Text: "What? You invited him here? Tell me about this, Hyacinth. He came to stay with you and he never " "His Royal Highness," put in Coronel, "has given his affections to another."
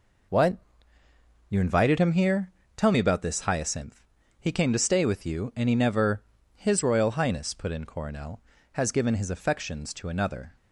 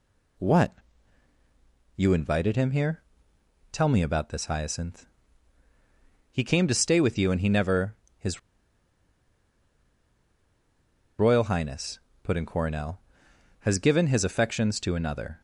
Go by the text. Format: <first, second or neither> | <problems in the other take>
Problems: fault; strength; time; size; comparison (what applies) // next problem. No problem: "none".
first | pauses between "His" and "Royal"; strong; at 8.3 s; 2.7 s long